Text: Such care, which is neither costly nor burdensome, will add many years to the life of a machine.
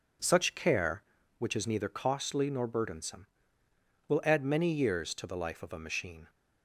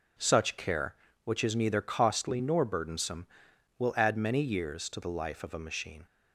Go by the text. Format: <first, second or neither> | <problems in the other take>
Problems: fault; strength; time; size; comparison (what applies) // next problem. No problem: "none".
neither | none